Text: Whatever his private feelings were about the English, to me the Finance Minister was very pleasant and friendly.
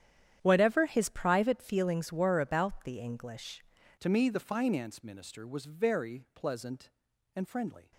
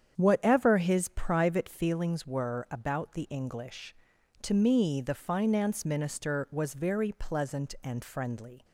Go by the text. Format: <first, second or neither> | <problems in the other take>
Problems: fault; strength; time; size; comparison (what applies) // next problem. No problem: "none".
second | starts louder than the rest; strong; until 1.4 s; 10 dB; strong in the second // changes voice at "to"; from 3.9 s on; 4.0 s long